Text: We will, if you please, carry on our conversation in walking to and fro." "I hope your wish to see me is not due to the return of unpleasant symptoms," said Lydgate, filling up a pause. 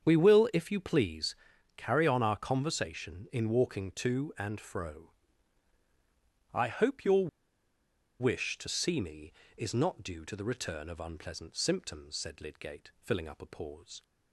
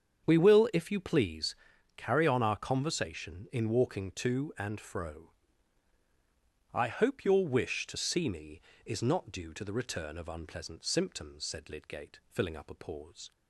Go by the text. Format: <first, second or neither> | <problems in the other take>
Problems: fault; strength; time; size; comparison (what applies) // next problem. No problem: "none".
second | starts louder than the rest; strong; until 1.0 s; 7.5 dB; strong in the second // pauses between "your" and "wish"; noticeable; at 7.2 s; 0.91 s long